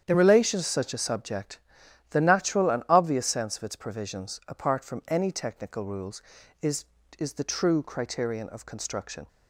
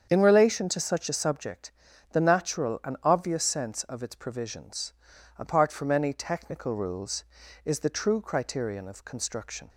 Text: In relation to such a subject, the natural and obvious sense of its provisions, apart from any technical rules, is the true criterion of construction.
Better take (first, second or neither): second